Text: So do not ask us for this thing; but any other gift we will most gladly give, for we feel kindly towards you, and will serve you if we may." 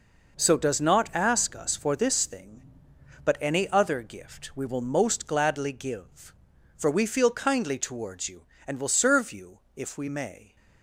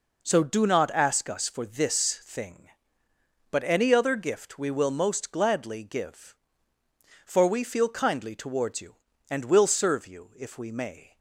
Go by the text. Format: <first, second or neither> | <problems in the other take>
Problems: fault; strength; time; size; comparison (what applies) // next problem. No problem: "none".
second | says "does" for "do"; at 0.5 s // pauses between "you" and "if"; slight; at 9.6 s; 0.16 s long